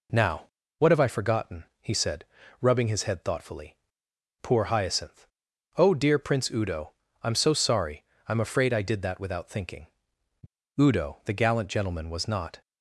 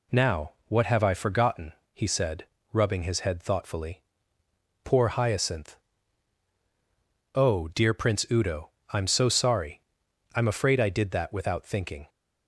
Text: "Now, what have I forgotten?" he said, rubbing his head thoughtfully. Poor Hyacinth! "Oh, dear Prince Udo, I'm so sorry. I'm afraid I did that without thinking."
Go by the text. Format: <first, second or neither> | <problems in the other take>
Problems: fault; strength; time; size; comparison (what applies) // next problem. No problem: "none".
second | goes on to say "Udo the gallant gentleman was not"; strong; from 10.7 s on; 1.8 s long